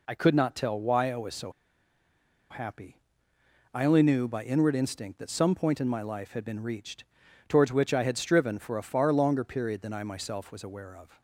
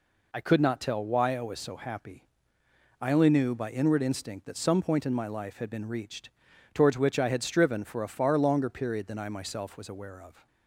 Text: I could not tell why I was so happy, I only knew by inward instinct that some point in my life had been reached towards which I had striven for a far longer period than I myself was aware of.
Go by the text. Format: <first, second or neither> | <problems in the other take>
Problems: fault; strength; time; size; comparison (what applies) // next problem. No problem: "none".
second | pauses between "so" and "happy"; at 1.5 s; 0.99 s long // pauses between "reached" and "towards"; at 7.0 s; 0.44 s long; also in the second